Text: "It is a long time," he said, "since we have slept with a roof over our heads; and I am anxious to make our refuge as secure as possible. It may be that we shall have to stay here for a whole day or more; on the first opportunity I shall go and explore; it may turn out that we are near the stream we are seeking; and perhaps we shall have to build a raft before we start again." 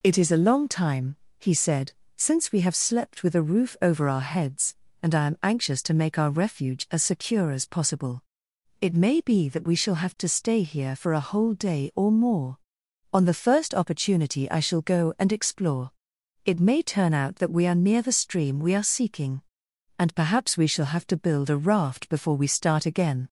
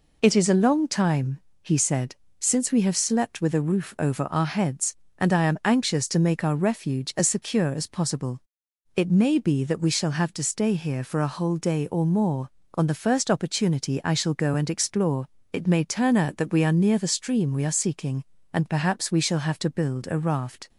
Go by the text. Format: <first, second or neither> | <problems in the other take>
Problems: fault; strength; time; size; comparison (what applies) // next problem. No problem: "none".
first | stops before "before we start again"; at 20.6 s